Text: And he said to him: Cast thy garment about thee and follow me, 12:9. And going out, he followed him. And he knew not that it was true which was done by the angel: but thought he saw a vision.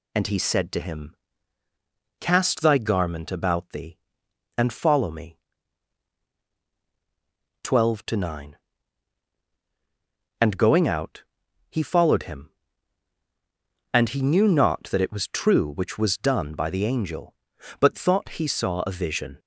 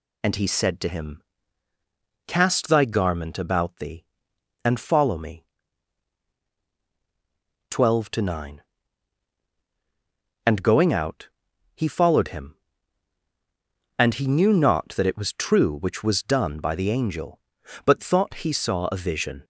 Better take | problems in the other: neither | none

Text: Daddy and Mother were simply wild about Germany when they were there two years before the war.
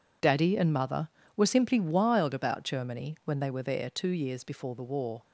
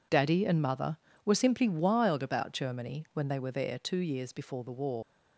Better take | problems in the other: first | leaves "war" unfinished; at 5.0 s; 100 ms

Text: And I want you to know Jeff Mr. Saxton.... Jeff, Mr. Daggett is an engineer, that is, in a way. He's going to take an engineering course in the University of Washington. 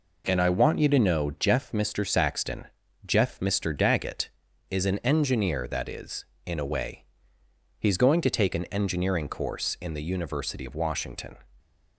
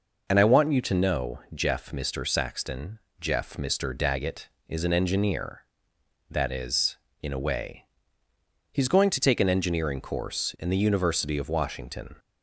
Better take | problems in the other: neither | none

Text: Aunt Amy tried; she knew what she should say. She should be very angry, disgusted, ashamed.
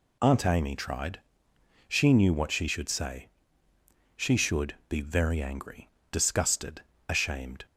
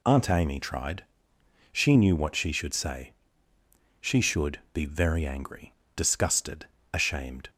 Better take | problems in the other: neither | none

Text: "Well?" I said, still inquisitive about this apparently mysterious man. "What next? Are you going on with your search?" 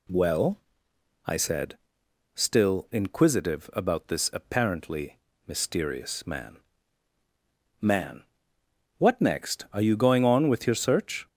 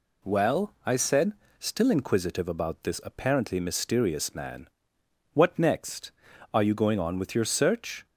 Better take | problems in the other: second | pauses between "apparently" and "mysterious"; slight; at 5.1 s; 0.30 s long // says "man" twice; at 7.8 s

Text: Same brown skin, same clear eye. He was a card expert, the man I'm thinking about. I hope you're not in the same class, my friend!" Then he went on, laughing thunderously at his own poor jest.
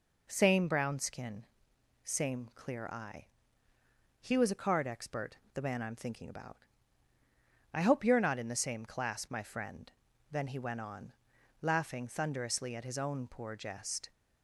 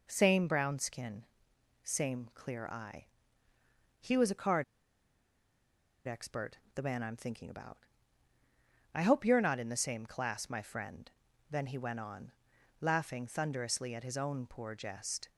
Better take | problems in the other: first | pauses between "card" and "expert"; strong; at 4.6 s; 1.4 s long

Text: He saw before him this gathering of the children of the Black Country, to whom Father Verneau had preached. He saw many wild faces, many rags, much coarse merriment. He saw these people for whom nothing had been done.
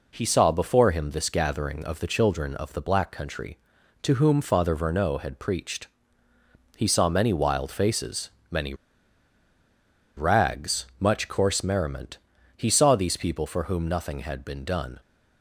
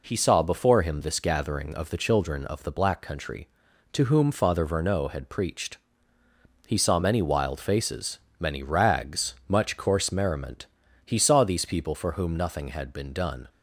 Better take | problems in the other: second | pauses between "many" and "rags"; strong; at 8.7 s; 1.4 s long

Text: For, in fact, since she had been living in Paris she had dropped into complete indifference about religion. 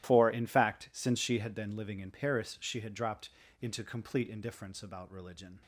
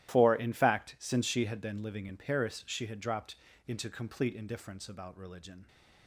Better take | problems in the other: neither | starts louder than the rest; strong; the same in both // pauses between "dropped" and "into"; slight; the same in both

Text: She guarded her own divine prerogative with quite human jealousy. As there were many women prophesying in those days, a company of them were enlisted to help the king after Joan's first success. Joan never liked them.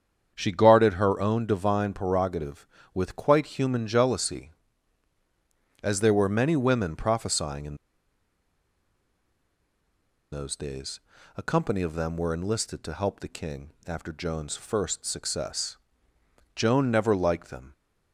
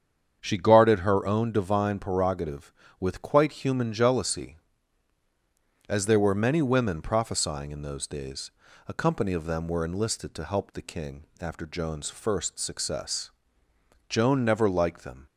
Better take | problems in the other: second | starts louder than the rest; strong; until 1.3 s; 7.5 dB; strong in the second // pauses between "in" and "those"; strong; at 7.7 s; 2.5 s long // pauses between "king" and "after"; slight; at 13.7 s; 0.16 s long; slight in the second

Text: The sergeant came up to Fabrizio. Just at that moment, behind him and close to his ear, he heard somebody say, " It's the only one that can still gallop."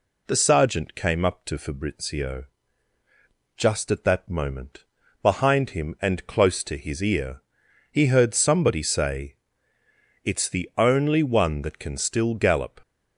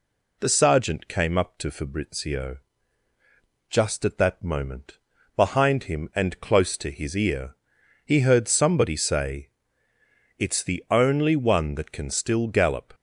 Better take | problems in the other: neither | none

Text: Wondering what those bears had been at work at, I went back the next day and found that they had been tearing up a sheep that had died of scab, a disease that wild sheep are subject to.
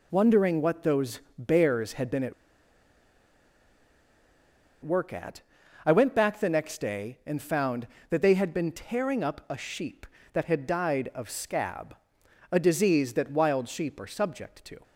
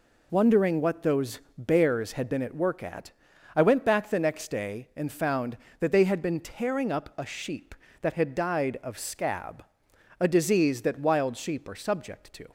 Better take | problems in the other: second | pauses between "those" and "bears"; slight; at 1.2 s; 0.16 s long; slight in the second // pauses between "at" and "work"; strong; at 2.3 s; 2.5 s long

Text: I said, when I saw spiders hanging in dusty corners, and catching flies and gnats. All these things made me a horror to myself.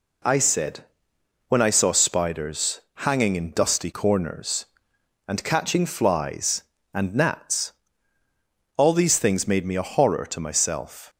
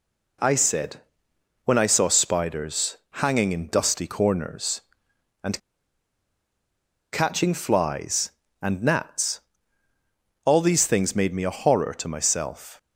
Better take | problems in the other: first | pauses between "spiders" and "hanging"; slight; at 2.9 s; 0.18 s long; slight in the first // pauses between "and" and "catching"; strong; at 5.5 s; 1.5 s long

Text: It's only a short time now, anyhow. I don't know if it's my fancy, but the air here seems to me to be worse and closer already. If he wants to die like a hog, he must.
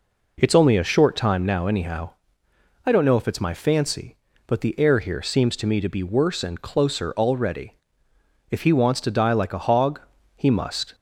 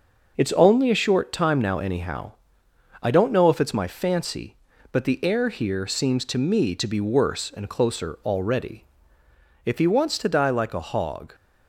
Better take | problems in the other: first | starts louder than the rest; noticeable; until 1.3 s; 6 dB // stops before "he must"; at 11.3 s

